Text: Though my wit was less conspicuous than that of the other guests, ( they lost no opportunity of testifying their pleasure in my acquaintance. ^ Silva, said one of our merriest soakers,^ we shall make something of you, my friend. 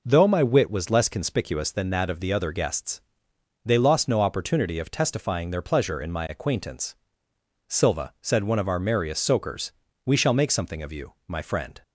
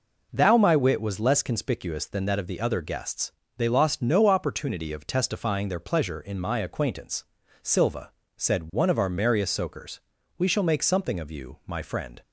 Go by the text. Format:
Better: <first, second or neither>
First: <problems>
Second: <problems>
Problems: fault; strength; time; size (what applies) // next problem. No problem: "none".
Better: first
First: none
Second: says "Thou" for "Though"; at 0.3 s